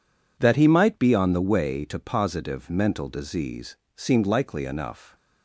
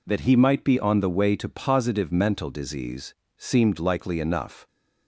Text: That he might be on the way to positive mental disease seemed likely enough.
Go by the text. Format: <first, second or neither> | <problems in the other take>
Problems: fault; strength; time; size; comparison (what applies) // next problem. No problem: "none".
neither | pauses between "disease" and "seemed"; slight; the same in both